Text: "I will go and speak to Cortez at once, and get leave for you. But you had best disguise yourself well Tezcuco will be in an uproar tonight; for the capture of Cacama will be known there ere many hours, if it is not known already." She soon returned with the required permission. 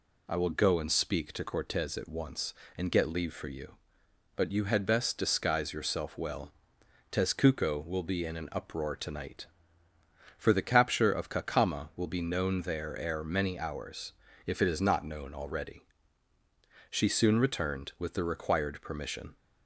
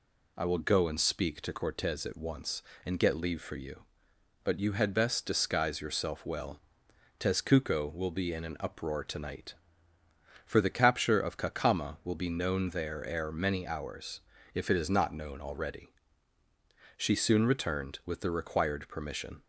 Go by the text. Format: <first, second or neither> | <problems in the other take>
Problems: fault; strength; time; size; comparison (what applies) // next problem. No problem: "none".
neither | pauses between "well" and "Tezcuco"; noticeable; the same in both